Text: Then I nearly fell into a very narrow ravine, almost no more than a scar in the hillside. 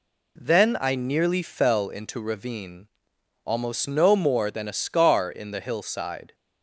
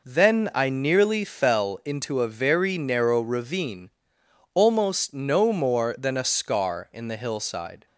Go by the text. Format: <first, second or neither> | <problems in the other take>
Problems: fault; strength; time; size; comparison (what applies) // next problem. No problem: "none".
second | skips "a very narrow"; at 2.2 s